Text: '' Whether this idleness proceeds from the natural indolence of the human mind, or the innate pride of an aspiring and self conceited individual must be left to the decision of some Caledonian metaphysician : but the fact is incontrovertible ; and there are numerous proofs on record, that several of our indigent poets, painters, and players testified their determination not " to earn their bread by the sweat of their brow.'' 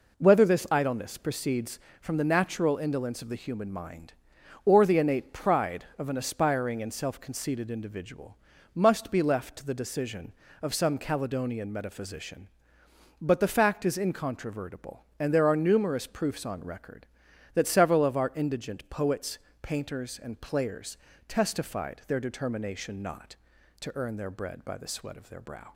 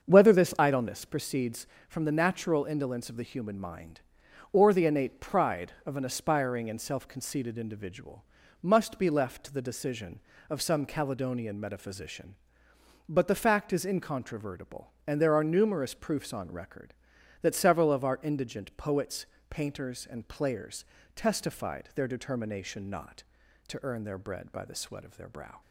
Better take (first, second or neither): first